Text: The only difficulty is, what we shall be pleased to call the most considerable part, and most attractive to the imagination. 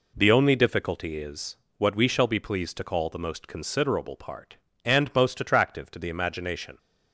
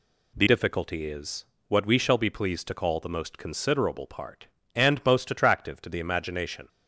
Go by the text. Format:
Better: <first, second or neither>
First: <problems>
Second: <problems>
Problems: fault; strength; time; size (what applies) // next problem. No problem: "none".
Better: first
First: none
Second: skips "only"; at 0.4 s